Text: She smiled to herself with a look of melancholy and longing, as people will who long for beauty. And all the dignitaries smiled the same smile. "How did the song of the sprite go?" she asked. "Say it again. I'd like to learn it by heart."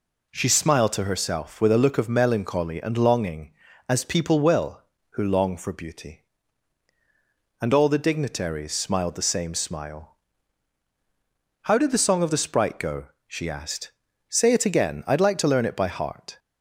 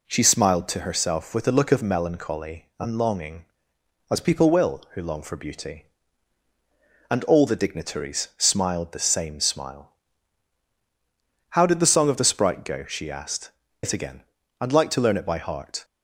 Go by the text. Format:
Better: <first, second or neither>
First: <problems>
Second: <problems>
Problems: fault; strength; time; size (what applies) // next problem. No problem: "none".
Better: first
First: none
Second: skips "Say"; at 13.6 s